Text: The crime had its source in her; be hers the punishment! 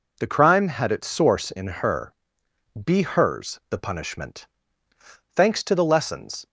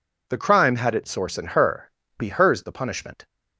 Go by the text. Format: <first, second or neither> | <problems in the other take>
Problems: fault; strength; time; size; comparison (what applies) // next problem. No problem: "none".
second | goes on to say "Thanks to the lessons"; noticeable; from 5.3 s on; 1.1 s long